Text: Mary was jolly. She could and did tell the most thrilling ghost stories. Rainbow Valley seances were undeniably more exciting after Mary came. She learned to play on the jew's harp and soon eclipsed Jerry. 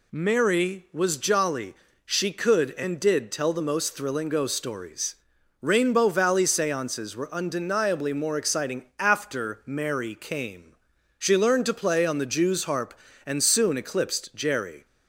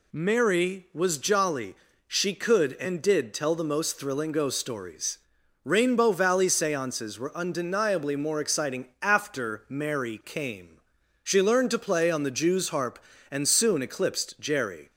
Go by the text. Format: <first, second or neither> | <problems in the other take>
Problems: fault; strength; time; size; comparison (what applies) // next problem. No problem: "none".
neither | none